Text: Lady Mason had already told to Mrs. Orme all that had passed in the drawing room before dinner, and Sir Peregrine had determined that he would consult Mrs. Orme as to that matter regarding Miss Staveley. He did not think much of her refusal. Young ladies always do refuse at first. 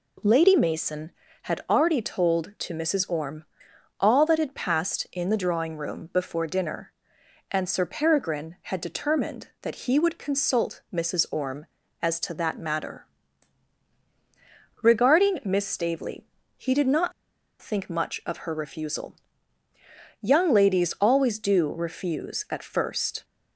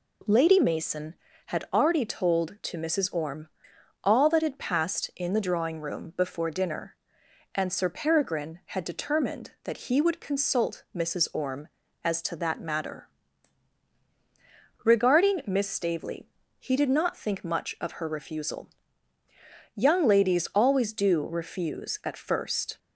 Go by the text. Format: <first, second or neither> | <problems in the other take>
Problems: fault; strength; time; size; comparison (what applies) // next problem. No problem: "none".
second | pauses between "Orme" and "all"; noticeable; at 3.4 s; 0.56 s long; noticeable in the second // pauses between "matter" and "regarding"; strong; at 13.0 s; 1.7 s long; strong in the second // pauses between "not" and "think"; noticeable; at 17.1 s; 0.50 s long